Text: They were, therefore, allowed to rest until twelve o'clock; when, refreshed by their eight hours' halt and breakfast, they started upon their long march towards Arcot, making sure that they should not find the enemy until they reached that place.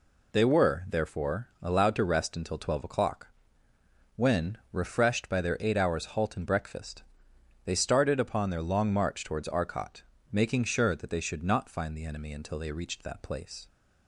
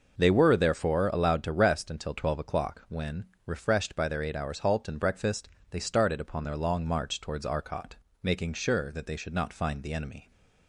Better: first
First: none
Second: stops before "until they reached that place"; at 10.3 s

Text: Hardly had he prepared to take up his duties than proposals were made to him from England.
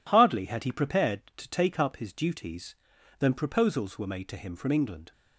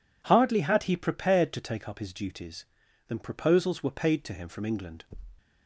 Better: first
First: none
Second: says "paid" for "made"; at 3.8 s

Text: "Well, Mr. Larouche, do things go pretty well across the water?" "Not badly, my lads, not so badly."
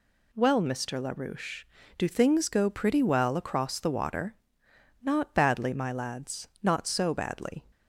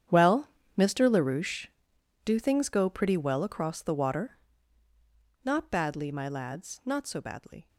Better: first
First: none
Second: gets quieter; strong; throughout; 16 dB

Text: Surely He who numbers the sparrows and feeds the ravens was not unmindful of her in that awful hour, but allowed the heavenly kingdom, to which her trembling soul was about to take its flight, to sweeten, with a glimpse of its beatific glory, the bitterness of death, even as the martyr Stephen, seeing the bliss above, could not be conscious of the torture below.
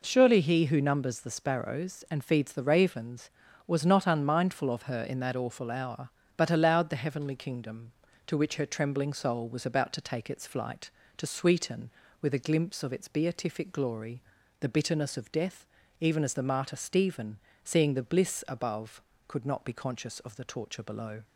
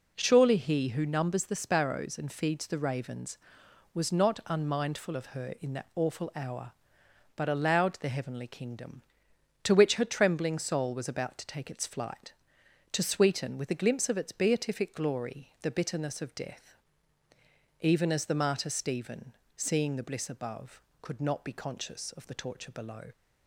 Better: neither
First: none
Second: none

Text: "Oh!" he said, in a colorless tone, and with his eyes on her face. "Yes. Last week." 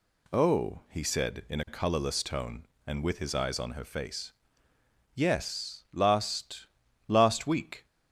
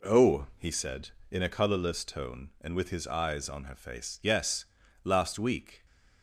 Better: second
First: says "Last" twice; at 7.0 s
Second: none

